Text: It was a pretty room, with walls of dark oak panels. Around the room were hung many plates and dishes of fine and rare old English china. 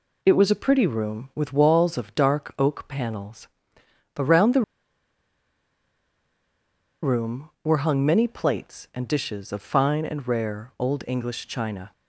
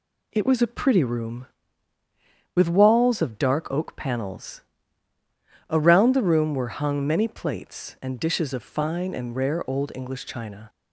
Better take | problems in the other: second | pauses between "the" and "room"; strong; at 4.6 s; 2.4 s long

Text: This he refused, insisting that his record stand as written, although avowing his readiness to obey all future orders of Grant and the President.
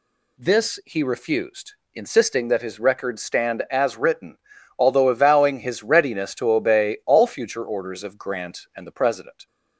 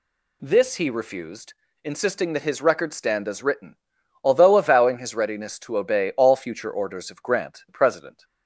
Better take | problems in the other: first | skips "and"; at 7.6 s

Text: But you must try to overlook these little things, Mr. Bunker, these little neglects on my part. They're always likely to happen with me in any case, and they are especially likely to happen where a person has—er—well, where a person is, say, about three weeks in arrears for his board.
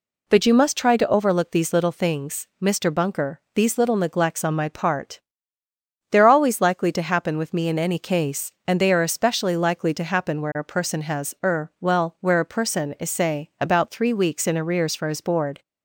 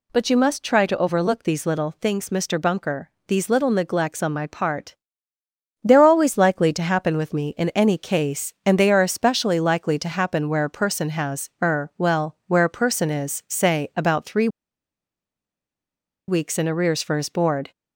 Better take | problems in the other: first | pauses between "three" and "weeks"; strong; at 14.4 s; 1.8 s long

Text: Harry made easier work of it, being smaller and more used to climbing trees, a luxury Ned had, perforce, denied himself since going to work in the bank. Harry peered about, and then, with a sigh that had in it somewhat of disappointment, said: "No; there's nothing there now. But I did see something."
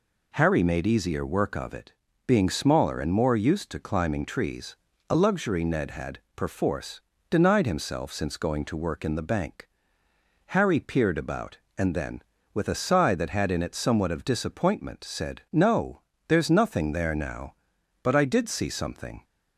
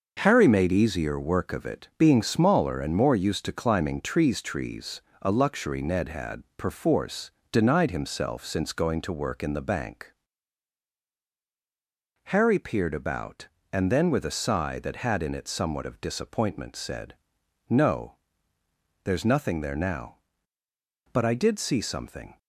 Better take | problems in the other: first | says "trees" twice; at 4.4 s

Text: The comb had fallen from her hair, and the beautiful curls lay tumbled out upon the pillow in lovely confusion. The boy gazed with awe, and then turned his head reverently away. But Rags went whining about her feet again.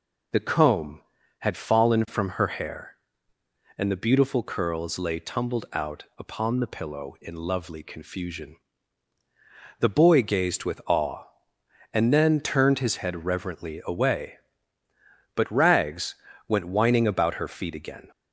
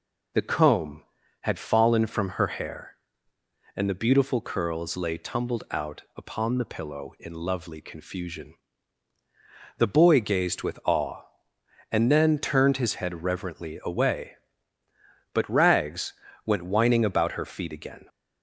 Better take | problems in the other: neither | pauses between "Rags" and "went"; slight; the same in both

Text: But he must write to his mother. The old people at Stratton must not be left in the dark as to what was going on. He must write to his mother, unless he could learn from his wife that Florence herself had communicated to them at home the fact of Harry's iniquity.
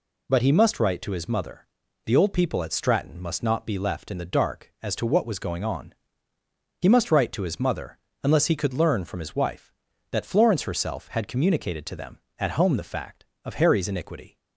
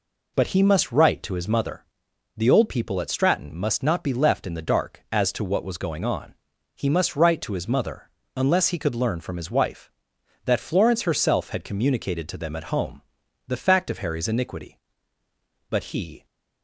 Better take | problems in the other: first | pauses between "home" and "the"; noticeable; at 13.0 s; 0.46 s long // goes on to say "But he"; from 15.7 s on; 0.54 s long

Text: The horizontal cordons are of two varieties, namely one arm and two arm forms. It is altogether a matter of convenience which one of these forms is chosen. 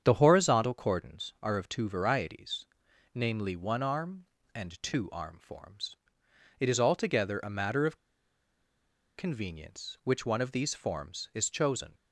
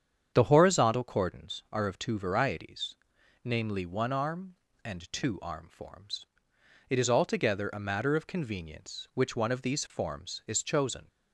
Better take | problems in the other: second | starts louder than the rest; strong; until 1.0 s; 8 dB; strong in the second // pauses between "of" and "convenience"; at 7.9 s; 1.2 s long

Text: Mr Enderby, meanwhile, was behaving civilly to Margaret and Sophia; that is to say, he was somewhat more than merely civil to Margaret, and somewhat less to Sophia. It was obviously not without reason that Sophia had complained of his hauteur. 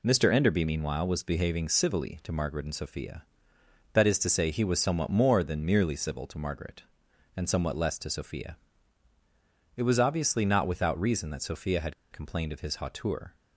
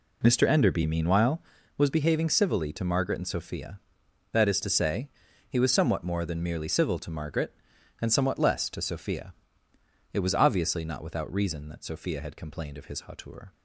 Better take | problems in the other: second | pauses between "had" and "complained"; slight; at 11.9 s; 0.18 s long

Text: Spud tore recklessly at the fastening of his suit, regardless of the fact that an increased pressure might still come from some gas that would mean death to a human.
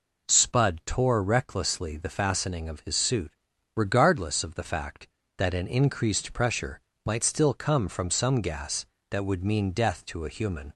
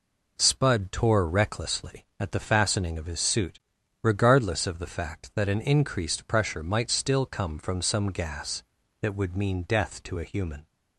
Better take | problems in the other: second | skips "at"; at 1.9 s // pauses between "pressure" and "might"; slight; at 6.7 s; 0.24 s long

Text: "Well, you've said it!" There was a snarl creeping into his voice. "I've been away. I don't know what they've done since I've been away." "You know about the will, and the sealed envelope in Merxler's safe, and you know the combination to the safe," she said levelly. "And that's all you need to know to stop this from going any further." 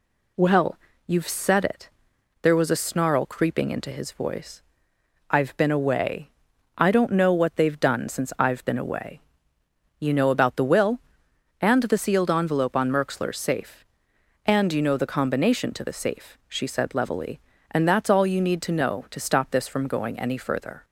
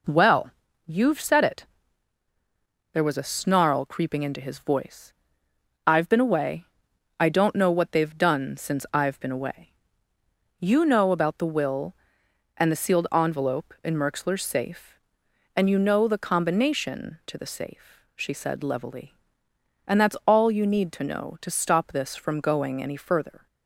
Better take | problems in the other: second | says "on" for "in"; at 12.7 s

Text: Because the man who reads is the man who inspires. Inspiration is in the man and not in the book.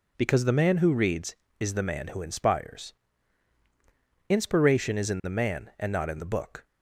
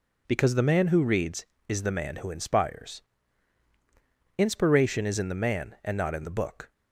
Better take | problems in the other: neither | none

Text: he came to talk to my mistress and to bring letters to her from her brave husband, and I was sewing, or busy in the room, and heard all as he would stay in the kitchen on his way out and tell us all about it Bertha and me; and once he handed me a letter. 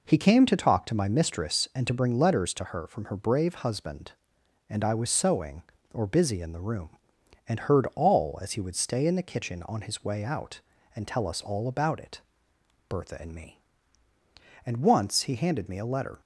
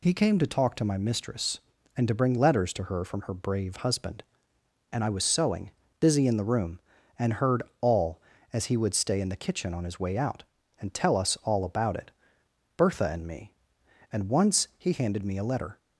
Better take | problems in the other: first | skips "or"; at 5.8 s // pauses between "heard" and "all"; slight; at 7.6 s; 0.16 s long // pauses between "it" and "Bertha"; noticeable; at 12.1 s; 0.64 s long; noticeable in the first

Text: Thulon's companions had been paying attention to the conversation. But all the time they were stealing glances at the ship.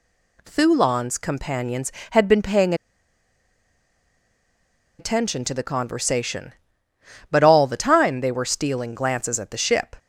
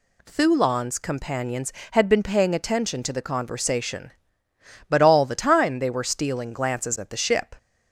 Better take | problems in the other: second | pauses between "paying" and "attention"; strong; at 2.7 s; 2.2 s long

